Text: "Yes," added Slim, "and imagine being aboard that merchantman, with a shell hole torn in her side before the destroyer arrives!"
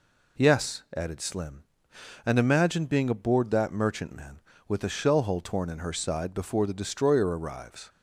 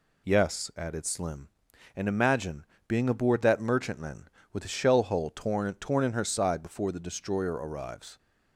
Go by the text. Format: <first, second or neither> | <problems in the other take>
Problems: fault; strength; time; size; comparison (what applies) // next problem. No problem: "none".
first | pauses between "imagine" and "being"; slight; at 2.6 s; 0.24 s long // says "torn" twice; at 5.7 s